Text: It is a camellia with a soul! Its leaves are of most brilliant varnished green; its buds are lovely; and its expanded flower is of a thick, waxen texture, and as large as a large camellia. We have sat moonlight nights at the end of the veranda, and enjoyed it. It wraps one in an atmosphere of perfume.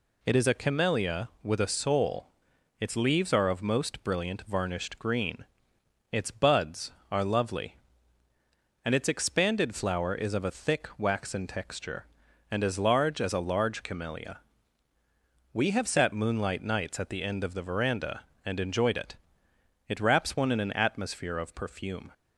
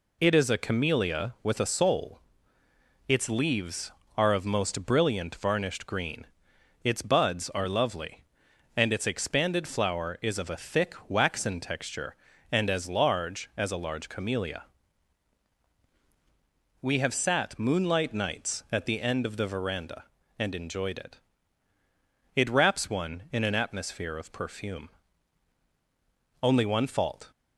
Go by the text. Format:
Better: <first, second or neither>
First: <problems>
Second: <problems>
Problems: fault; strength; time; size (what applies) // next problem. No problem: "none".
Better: first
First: none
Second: goes on to say "Only one fault"; noticeable; from 26.4 s on; 0.90 s long